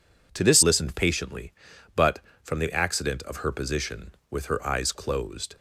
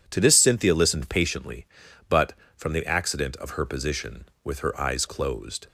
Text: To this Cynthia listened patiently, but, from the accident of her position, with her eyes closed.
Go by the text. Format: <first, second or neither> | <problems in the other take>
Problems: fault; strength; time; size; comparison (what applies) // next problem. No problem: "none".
second | skips "Cynthia"; at 0.6 s